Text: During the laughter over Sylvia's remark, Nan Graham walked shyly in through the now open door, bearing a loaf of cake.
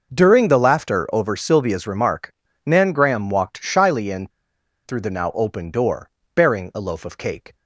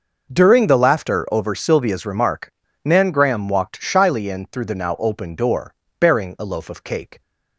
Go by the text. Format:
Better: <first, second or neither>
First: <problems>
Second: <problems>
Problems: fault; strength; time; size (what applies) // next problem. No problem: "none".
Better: second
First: pauses between "in" and "through"; noticeable; at 4.2 s; 0.56 s long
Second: none